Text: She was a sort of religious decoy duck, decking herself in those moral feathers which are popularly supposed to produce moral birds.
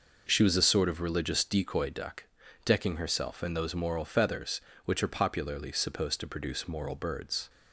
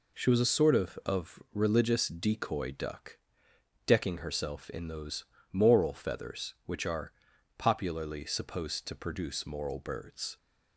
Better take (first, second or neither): first